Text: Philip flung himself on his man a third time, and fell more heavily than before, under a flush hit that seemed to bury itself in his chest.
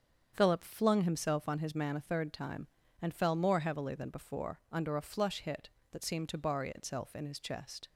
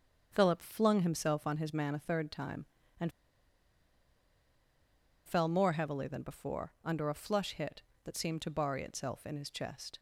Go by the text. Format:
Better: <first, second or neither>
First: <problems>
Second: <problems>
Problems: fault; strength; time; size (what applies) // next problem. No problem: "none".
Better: first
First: starts louder than the rest; strong; until 1.3 s; 7.5 dB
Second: starts louder than the rest; strong; until 1.3 s; 7.5 dB // pauses between "and" and "fell"; strong; at 3.1 s; 2.1 s long